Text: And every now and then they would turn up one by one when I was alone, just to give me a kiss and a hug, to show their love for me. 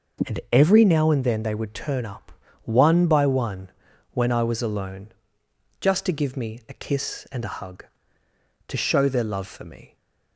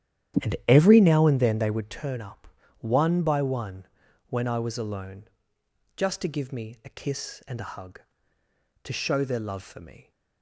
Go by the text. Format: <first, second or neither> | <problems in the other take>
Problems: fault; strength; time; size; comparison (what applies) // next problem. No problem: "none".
first | starts louder than the rest; strong; until 2.0 s; 10.5 dB // pauses between "up" and "one"; slight; at 2.4 s; 0.32 s long; slight in the first // pauses between "one" and "when"; at 3.8 s; 0.44 s long; also in the first